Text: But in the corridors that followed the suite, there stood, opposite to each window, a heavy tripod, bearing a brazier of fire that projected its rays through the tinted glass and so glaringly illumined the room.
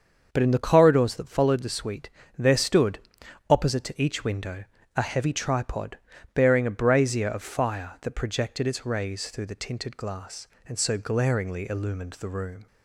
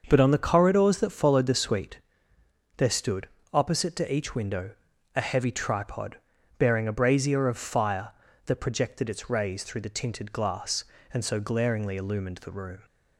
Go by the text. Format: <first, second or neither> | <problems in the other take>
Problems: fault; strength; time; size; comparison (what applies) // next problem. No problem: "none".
first | starts louder than the rest; until 1.0 s; 6.5 dB; also in the first // says "on" for "in"; at 0.1 s